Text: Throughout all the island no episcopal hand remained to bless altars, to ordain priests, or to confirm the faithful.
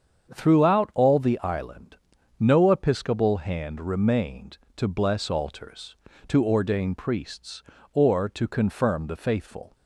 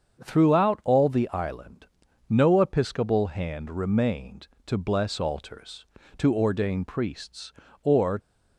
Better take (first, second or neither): first